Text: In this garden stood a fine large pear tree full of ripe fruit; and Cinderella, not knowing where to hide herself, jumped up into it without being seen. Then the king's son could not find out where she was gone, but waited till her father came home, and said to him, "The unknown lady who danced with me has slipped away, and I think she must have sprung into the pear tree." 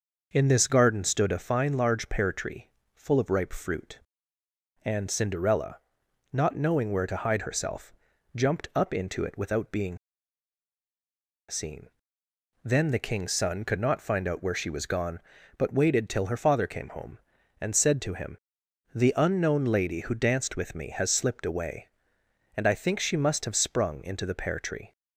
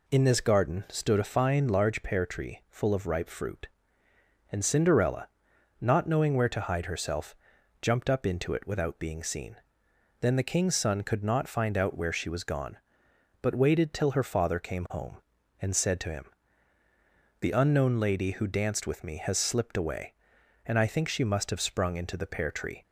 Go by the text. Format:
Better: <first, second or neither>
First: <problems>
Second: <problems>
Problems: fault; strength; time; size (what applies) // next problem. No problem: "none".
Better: second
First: pauses between "tree" and "full"; slight; at 2.6 s; 0.24 s long // pauses between "being" and "seen"; strong; at 9.9 s; 1.5 s long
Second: none